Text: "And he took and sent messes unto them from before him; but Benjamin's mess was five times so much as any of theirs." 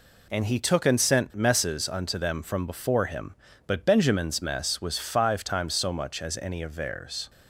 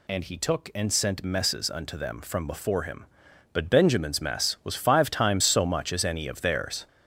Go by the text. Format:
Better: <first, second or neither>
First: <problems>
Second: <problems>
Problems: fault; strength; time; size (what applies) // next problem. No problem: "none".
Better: first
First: none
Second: gets louder; noticeable; throughout; 6 dB